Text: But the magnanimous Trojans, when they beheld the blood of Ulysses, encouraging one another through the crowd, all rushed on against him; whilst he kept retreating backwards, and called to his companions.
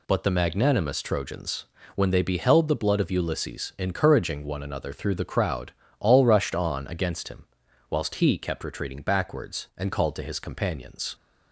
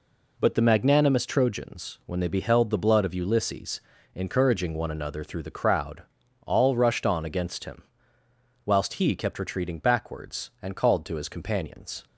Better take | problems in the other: neither | none

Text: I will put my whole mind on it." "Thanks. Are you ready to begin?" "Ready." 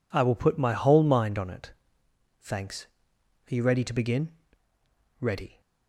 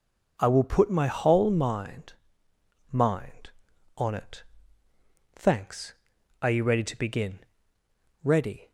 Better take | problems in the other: first | says "mind" twice; at 2.9 s

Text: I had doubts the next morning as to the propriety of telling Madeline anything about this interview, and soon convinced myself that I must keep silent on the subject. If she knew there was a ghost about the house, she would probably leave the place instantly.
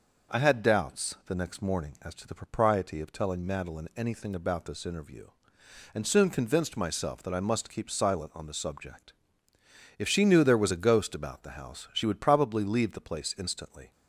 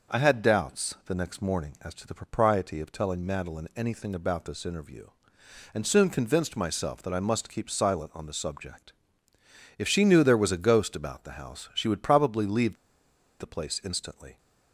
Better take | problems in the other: first | pauses between "leave" and "the"; noticeable; at 12.7 s; 0.66 s long

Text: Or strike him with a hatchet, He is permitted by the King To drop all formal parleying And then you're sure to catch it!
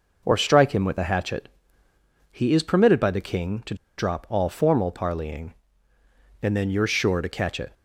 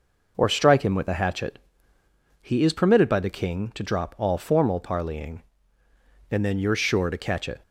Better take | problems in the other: second | pauses between "To" and "drop"; slight; at 3.7 s; 0.23 s long

